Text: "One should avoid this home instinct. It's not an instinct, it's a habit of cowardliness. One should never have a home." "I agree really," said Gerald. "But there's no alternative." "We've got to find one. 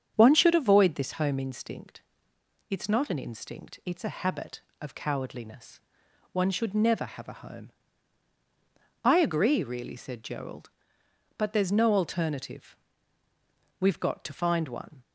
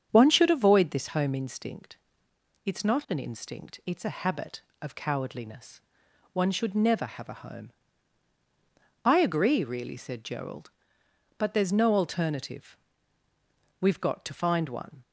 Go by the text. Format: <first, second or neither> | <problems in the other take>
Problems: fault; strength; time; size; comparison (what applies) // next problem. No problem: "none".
neither | starts louder than the rest; strong; the same in both